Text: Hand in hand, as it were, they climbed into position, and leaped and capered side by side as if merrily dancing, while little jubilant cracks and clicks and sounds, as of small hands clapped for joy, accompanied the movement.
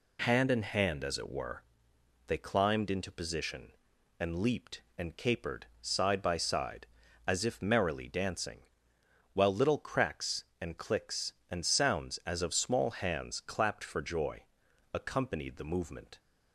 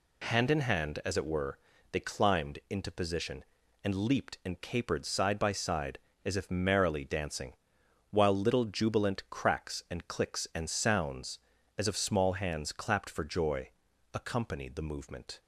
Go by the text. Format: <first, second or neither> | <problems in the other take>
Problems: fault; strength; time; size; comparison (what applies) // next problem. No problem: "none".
second | pauses between "capered" and "side"; slight; at 5.6 s; 0.16 s long // skips "jubilant"; at 9.7 s